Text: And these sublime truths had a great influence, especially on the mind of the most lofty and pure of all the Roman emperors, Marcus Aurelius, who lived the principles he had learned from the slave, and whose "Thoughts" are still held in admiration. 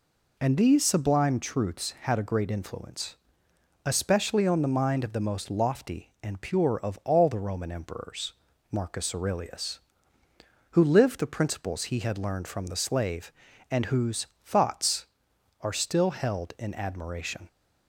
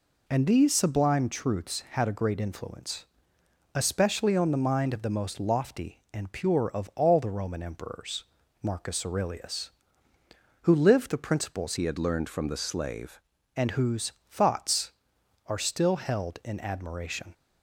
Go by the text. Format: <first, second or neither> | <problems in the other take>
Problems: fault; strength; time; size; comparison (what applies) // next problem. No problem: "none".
first | changes voice from "he" to "slave"; from 11.7 to 13.1 s; 1.4 s long // pauses between "whose" and "Thoughts"; slight; at 14.1 s; 0.18 s long; slight in the first